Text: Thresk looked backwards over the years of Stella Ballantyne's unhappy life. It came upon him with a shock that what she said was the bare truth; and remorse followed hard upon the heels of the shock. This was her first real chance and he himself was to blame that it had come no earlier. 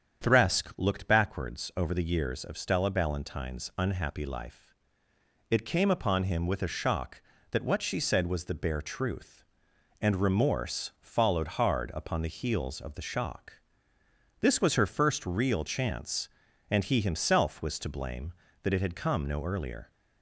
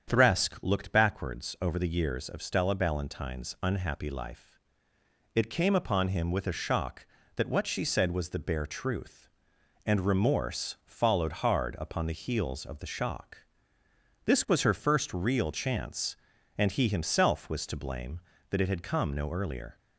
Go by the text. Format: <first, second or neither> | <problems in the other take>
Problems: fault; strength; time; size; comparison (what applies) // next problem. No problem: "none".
neither | starts louder than the rest; strong; the same in both